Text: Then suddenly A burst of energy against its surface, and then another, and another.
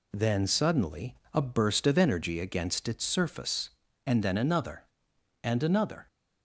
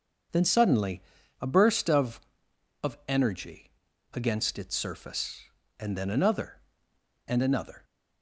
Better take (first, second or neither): first